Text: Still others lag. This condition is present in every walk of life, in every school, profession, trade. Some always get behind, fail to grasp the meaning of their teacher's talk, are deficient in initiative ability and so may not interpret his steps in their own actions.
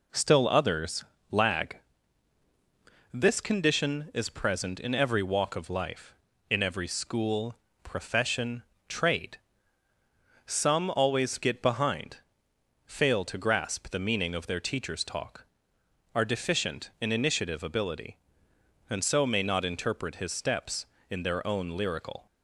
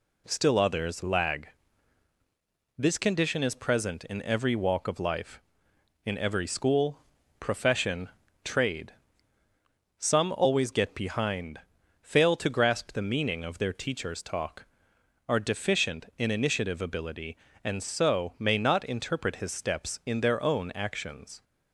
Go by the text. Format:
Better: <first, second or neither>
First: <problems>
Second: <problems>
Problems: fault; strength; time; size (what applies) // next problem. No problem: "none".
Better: second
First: pauses between "others" and "lag"; slight; at 1.0 s; 0.26 s long // says "lyrical" for "actions"; at 21.7 s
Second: none